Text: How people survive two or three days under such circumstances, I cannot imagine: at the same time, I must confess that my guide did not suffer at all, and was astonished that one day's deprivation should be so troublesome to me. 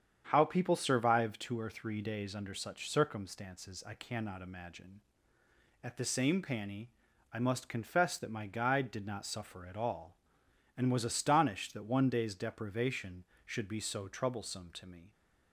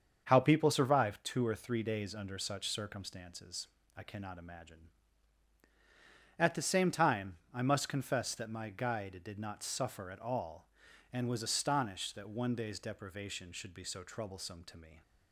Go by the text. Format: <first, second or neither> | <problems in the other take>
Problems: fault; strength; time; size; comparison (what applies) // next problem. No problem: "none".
second | starts louder than the rest; strong; until 1.3 s; 8.5 dB; also in the second // says "panny" for "time"; at 6.3 s